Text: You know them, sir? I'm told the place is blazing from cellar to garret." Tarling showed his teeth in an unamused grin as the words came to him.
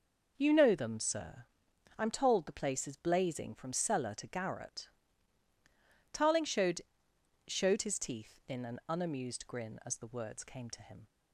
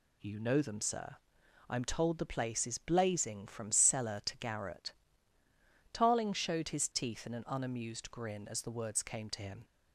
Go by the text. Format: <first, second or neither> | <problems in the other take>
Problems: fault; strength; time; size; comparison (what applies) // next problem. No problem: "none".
second | says "showed" twice; at 7.4 s